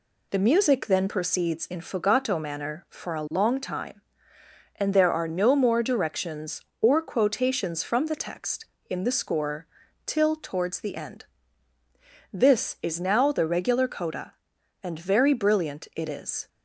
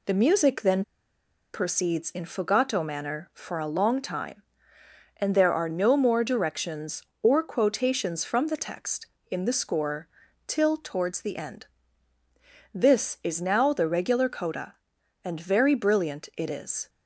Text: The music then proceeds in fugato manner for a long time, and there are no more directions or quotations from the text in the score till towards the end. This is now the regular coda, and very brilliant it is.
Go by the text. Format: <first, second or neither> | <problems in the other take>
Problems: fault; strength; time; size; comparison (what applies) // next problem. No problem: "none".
first | pauses between "then" and "proceeds"; noticeable; at 0.8 s; 0.72 s long // pauses between "score" and "till"; at 10.0 s; 0.40 s long; also in the first